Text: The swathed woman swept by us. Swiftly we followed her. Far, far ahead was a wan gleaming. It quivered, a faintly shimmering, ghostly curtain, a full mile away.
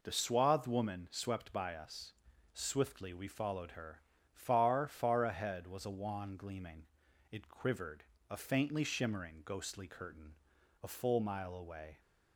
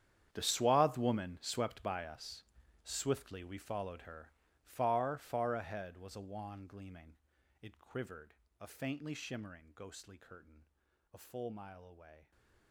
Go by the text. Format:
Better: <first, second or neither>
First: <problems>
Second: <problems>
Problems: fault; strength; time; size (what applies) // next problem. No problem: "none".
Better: first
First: none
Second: gets quieter; strong; throughout; 18 dB